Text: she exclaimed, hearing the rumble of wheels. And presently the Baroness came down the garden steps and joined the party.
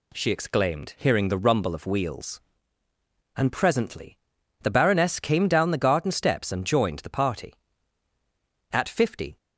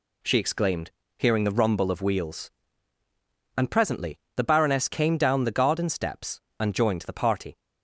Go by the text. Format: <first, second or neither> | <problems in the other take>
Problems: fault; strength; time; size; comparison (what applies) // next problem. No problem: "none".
second | pauses between "presently" and "the"; at 4.1 s; 0.42 s long; slight in the second // goes on to say "At fifty"; noticeable; from 8.7 s on; 0.66 s long